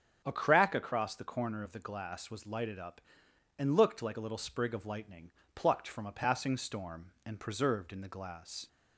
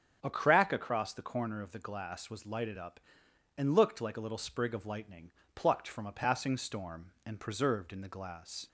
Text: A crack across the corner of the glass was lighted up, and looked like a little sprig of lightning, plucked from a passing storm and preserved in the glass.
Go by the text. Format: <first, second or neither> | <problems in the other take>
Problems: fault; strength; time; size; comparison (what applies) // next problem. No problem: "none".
neither | starts louder than the rest; strong; the same in both